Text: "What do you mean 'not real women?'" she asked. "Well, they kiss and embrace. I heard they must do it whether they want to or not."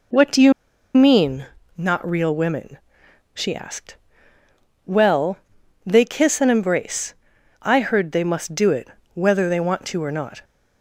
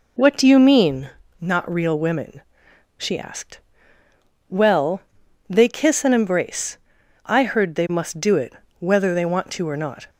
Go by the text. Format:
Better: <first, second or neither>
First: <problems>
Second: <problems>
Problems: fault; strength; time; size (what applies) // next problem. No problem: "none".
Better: second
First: pauses between "you" and "mean"; at 0.5 s; 0.43 s long // pauses between "mean" and "not"; slight; at 1.4 s; 0.28 s long // pauses between "it" and "whether"; slight; at 8.8 s; 0.26 s long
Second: pauses between "mean" and "not"; slight; at 1.1 s; 0.28 s long // pauses between "it" and "whether"; slight; at 8.5 s; 0.26 s long